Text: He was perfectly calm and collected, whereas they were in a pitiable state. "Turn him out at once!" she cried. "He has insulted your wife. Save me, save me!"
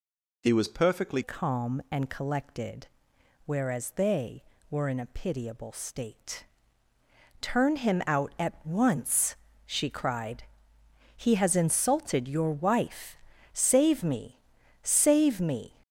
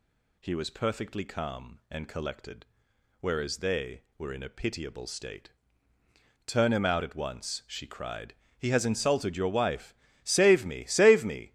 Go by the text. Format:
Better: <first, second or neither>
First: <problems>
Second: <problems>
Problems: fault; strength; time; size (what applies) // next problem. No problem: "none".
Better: second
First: changes voice at "calm"; from 1.2 s on; 14.5 s long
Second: none